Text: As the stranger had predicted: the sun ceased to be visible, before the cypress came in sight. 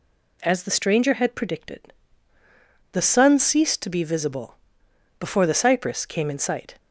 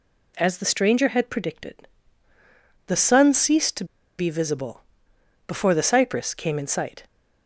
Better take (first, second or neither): first